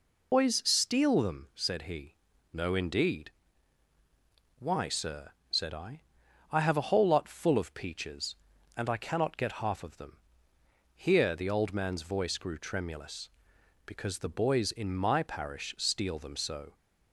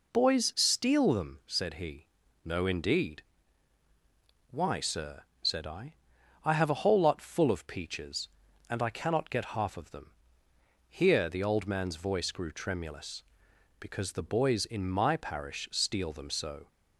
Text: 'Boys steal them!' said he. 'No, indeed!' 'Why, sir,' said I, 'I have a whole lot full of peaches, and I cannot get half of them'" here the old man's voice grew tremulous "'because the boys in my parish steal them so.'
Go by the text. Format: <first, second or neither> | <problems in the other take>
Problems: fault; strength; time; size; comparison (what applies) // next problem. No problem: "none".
second | loses the start of "Boys"; at 0.3 s; 100 ms // pauses between "them" and "here"; noticeable; at 10.1 s; 0.78 s long; noticeable in the second